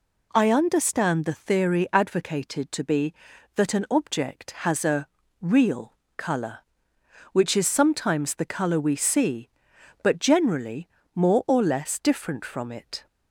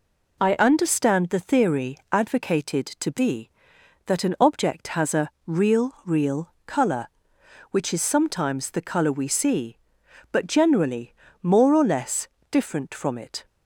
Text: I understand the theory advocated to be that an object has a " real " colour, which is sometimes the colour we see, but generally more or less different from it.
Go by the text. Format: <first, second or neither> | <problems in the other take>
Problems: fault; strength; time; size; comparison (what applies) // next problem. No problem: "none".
first | pauses between "theory" and "advocated"; slight; at 1.9 s; 0.16 s long // says "real" twice; at 6.0 s // pauses between "generally" and "more"; slight; at 11.1 s; 0.30 s long; slight in the first // pauses between "less" and "different"; slight; at 12.2 s; 0.22 s long